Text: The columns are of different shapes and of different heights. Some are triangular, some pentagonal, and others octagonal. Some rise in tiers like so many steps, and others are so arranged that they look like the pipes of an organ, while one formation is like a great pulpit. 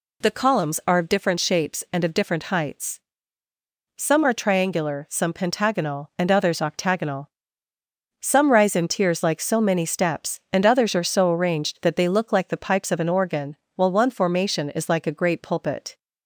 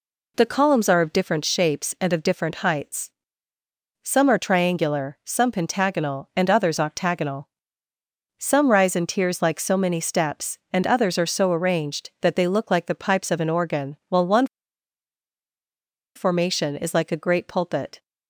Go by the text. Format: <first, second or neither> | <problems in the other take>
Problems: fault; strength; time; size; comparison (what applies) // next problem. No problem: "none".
first | pauses between "one" and "formation"; strong; at 14.4 s; 1.6 s long